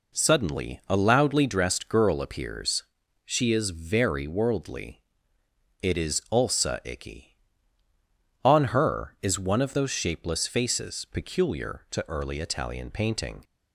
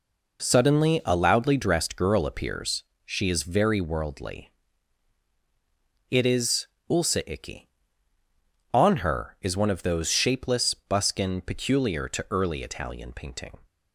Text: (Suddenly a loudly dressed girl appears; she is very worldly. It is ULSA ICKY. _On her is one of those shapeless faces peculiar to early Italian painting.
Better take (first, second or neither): first